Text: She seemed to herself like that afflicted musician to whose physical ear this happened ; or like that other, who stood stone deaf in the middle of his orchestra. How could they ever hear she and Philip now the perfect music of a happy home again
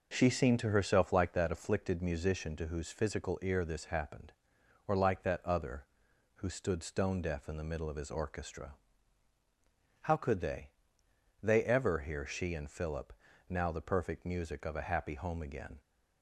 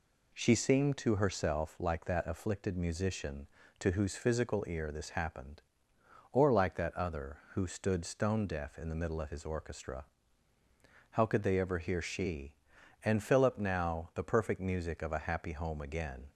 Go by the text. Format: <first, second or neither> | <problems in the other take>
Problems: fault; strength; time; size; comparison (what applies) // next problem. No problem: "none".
second | says "they" twice; at 11.4 s // pauses between "Philip" and "now"; slight; at 13.1 s; 0.34 s long